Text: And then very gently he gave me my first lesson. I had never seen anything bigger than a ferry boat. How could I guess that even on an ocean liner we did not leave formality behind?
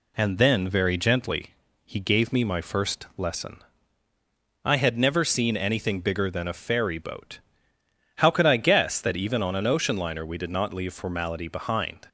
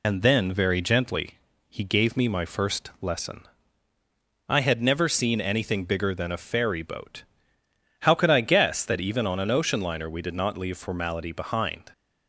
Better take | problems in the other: first | loses the start of "And"; at 0.0 s; 50 ms // pauses between "gently" and "he"; slight; at 1.3 s; 0.30 s long; slight in the first

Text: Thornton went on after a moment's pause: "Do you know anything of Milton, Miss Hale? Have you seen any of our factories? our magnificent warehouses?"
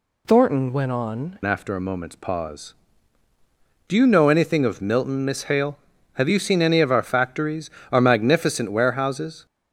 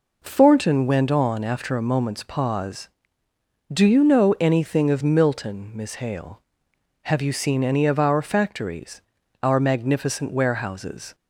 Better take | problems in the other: second | changes voice at "after"; from 1.4 s on; 8.0 s long

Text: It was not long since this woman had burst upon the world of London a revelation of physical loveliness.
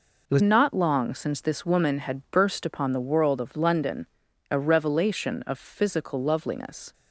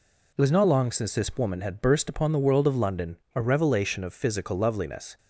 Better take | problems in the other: second | changes voice at "not"; from 0.4 s on; 6.5 s long // pauses between "London" and "a"; at 4.0 s; 0.44 s long; slight in the second

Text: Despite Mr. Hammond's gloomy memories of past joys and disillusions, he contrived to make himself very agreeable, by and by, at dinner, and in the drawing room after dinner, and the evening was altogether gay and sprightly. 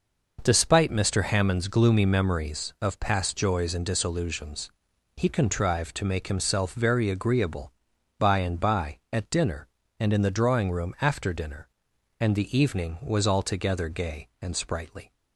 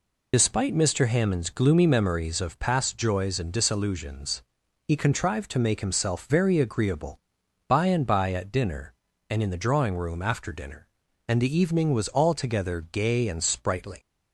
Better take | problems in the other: first | loses the start of "Despite"; at 0.3 s; 50 ms

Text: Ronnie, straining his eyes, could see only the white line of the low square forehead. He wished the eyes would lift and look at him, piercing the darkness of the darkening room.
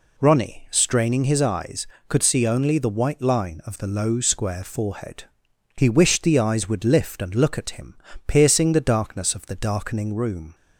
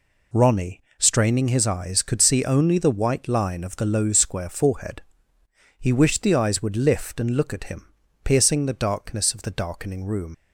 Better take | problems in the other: first | leaves "room" unfinished; at 10.3 s; 105 ms

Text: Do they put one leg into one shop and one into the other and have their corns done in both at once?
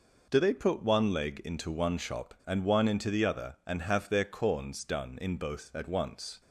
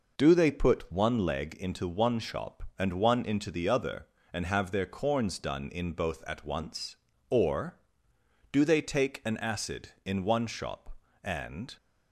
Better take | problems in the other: first | goes on to say "Or do they take an acid in one shop and"; strong; from 7.3 s on; 4.4 s long

